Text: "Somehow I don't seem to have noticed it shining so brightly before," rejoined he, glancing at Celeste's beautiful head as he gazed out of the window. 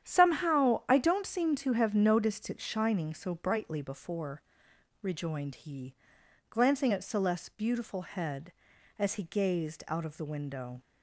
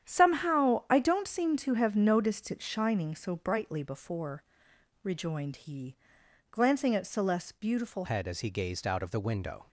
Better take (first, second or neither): first